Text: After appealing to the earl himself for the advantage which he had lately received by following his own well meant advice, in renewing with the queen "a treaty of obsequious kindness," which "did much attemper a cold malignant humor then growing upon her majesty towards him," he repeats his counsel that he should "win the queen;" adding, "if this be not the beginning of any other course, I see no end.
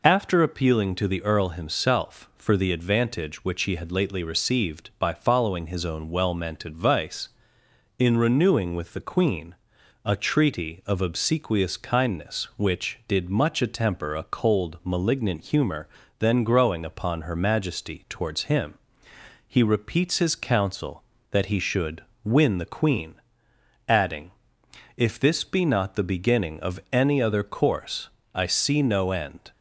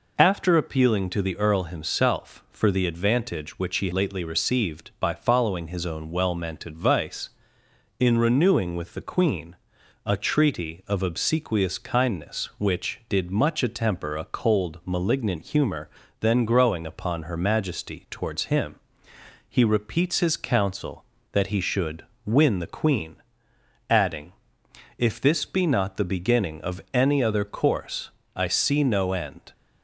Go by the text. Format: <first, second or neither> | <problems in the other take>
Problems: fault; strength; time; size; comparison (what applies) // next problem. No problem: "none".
first | skips "had"; at 3.9 s // pauses between "queen" and "a"; noticeable; at 9.5 s; 0.50 s long; noticeable in the first // pauses between "humor" and "then"; slight; at 15.8 s; 0.30 s long; slight in the first // pauses between "should" and "win"; slight; at 22.0 s; 0.22 s long; slight in the first